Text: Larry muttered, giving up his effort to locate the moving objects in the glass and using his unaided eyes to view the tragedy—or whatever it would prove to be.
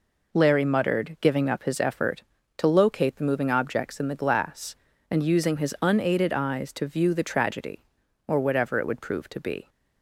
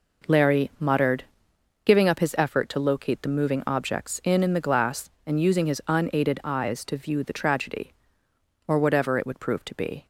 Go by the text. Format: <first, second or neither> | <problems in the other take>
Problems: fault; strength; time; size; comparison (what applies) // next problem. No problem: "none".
first | says "in" twice; at 4.4 s